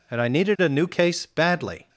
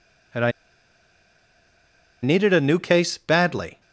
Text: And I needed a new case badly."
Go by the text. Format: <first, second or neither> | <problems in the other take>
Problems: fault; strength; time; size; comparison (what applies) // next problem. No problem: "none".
first | pauses between "I" and "needed"; strong; at 0.5 s; 1.7 s long